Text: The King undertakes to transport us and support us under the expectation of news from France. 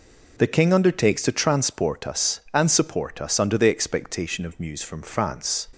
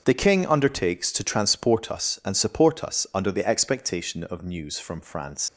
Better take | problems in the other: first | starts louder than the rest; until 1.0 s; 7 dB // leaves "France" unfinished; at 5.4 s; 115 ms

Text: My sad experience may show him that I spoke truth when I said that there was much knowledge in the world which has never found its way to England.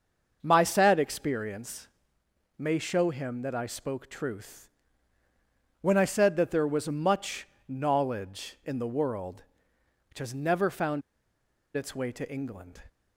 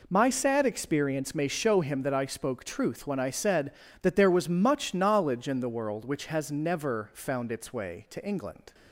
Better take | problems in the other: second | starts louder than the rest; until 1.4 s; 6.5 dB // pauses between "experience" and "may"; noticeable; at 1.8 s; 0.70 s long // pauses between "truth" and "when"; at 4.6 s; 1.1 s long // pauses between "much" and "knowledge"; slight; at 7.4 s; 0.22 s long // pauses between "found" and "its"; noticeable; at 11.0 s; 0.75 s long

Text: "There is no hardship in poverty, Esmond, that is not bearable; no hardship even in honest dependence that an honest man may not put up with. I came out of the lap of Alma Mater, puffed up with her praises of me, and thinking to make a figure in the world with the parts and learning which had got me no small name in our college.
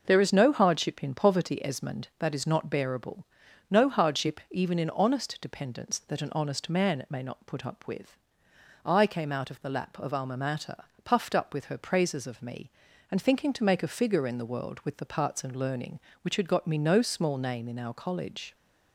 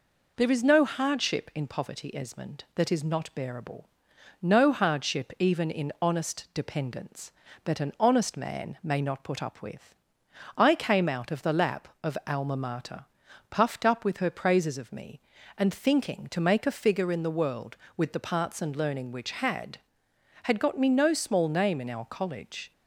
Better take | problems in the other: first | says "had" twice; at 20.4 s

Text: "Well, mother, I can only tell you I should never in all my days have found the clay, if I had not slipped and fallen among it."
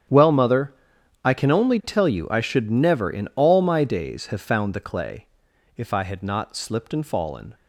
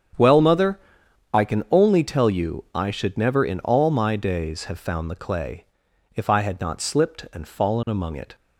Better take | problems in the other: second | starts louder than the rest; strong; until 1.5 s; 9 dB; strong in the second // stops before "among it"; at 7.5 s

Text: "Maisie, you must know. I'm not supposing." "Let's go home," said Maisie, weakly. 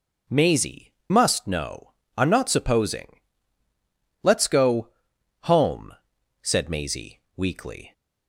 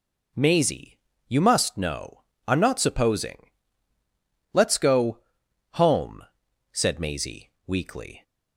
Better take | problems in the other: second | skips "you"; at 1.0 s // pauses between "go" and "home"; noticeable; at 4.8 s; 0.54 s long; noticeable in the second

